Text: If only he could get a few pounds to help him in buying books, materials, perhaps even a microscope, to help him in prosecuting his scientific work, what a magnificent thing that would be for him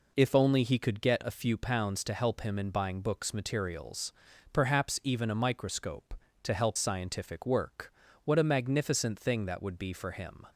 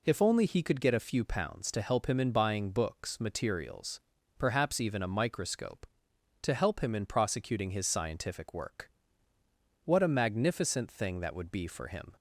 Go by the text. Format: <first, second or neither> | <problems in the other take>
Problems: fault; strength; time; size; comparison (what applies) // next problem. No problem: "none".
second | skips "him in prosecuting his"; at 6.7 s